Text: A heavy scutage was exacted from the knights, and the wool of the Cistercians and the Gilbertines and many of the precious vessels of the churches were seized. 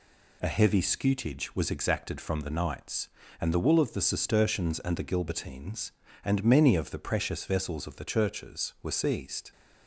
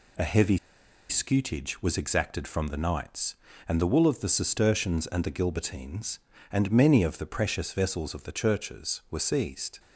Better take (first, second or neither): first